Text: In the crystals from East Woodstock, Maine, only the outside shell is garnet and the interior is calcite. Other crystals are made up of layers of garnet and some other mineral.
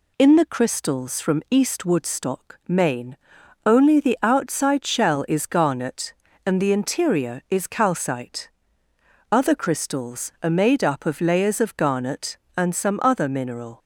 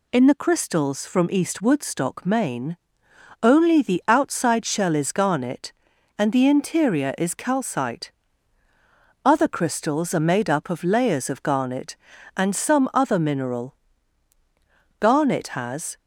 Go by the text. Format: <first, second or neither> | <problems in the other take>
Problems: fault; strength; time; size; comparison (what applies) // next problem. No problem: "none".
first | goes on to say "Garnet has"; noticeable; from 14.9 s on; 0.98 s long